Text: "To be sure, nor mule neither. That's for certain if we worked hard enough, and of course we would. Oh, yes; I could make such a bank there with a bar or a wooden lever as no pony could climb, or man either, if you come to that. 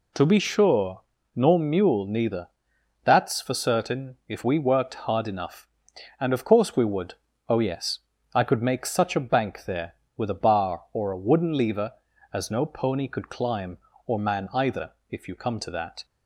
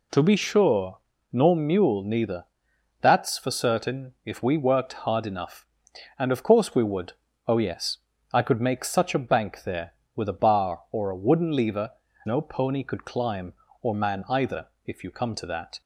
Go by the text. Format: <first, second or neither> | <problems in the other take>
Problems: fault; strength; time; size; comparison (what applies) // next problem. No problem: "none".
first | skips "as"; at 12.0 s